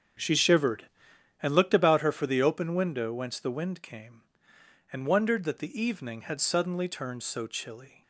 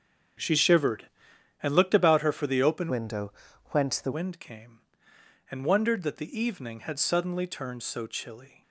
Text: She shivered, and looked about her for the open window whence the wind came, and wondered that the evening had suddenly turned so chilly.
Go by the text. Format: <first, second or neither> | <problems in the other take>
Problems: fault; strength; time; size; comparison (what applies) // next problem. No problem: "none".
first | starts louder than the rest; until 1.9 s; 7 dB; also in the first // changes voice from "window" to "the"; from 2.8 to 4.1 s; 1.3 s long // pauses between "window" and "whence"; at 3.3 s; 0.40 s long